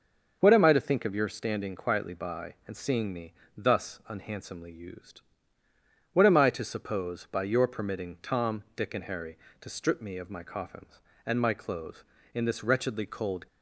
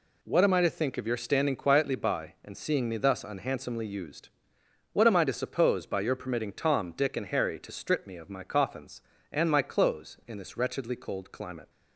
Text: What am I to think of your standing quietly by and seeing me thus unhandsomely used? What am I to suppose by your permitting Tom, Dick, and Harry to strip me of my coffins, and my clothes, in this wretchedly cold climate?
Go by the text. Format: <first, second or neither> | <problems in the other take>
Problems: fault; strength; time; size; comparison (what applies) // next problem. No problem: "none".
second | starts louder than the rest; until 1.4 s; 6 dB // pauses between "me" and "thus"; slight; at 3.3 s; 0.24 s long // stops before "climate"; at 13.4 s